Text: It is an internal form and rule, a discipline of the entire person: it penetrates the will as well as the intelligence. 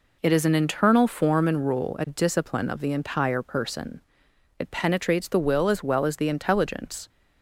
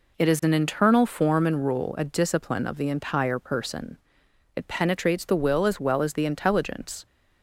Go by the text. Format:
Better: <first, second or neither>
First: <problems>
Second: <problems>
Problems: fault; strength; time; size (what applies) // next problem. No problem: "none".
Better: neither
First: none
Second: none